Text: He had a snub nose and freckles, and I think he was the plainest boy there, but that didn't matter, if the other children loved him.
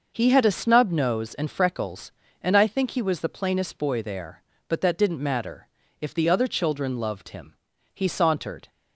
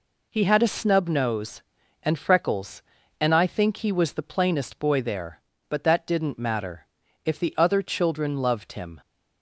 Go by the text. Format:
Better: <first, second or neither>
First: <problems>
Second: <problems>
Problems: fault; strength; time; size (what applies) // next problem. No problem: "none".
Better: second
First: goes on to say "He sauntered"; noticeable; from 7.9 s on; 0.74 s long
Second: none